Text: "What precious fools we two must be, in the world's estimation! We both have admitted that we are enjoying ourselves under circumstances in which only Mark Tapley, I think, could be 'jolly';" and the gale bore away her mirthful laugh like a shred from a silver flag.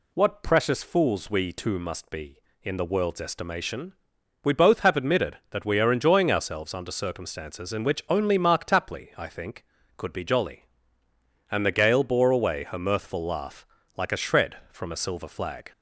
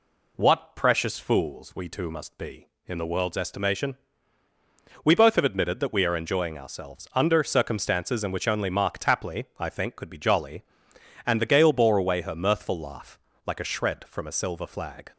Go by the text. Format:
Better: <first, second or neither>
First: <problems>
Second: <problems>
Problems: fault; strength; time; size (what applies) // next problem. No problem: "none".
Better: neither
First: pauses between "laugh" and "like"; slight; at 13.6 s; 0.30 s long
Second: pauses between "laugh" and "like"; slight; at 13.1 s; 0.28 s long